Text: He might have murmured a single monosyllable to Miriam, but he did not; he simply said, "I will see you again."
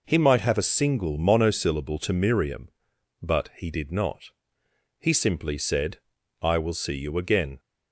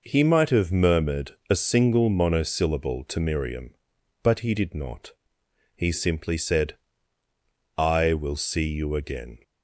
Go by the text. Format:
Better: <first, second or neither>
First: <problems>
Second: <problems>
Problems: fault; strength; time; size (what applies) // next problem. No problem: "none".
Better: second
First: skips "murmured"; at 0.5 s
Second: none